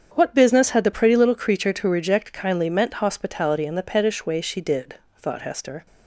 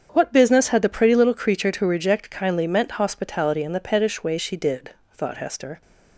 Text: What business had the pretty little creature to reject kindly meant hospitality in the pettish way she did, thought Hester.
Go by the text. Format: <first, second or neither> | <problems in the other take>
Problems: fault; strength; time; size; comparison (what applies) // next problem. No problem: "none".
neither | starts louder than the rest; strong; the same in both